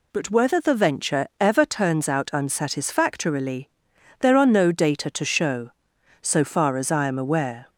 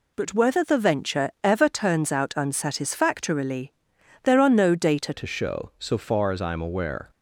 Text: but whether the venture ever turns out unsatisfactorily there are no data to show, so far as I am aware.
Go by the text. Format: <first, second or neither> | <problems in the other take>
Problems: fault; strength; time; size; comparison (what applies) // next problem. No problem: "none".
first | pauses between "unsatisfactorily" and "there"; noticeable; at 3.7 s; 0.52 s long; noticeable in the first // changes voice at "to"; from 5.1 s on; 1.9 s long